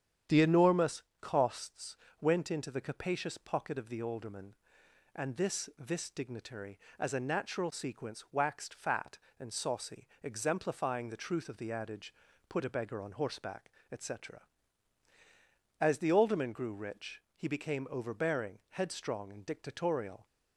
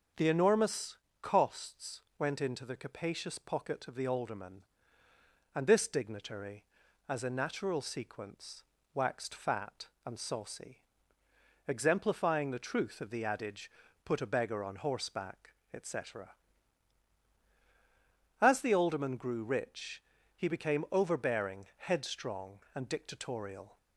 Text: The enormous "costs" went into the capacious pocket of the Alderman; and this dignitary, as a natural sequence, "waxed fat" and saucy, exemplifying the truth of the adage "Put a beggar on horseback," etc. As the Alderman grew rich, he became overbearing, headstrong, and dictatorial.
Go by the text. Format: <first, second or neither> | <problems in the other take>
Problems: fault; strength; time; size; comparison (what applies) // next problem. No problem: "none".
second | starts louder than the rest; strong; until 1.4 s; 9 dB; strong in the second // pauses between "enormous" and "costs"; slight; at 1.0 s; 0.18 s long; slight in the second // pauses between "costs" and "went"; slight; at 1.9 s; 0.22 s long; slight in the second // says "this" twice; at 5.7 s // pauses between "adage" and "Put"; at 12.1 s; 0.38 s long; slight in the second